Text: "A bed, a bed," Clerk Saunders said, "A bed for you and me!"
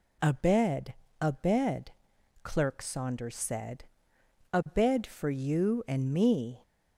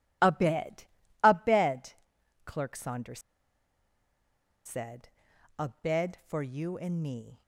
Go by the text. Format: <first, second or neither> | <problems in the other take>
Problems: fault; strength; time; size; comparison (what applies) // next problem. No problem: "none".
first | pauses between "Saunders" and "said"; strong; at 3.1 s; 1.4 s long